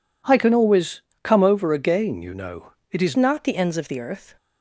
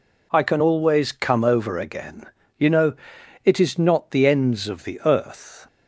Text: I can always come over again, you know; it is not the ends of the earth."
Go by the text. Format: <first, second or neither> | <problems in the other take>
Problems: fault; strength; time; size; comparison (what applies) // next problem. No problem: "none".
second | pauses between "always" and "come"; slight; at 1.0 s; 0.22 s long // changes voice at "not"; from 3.1 s on; 1.2 s long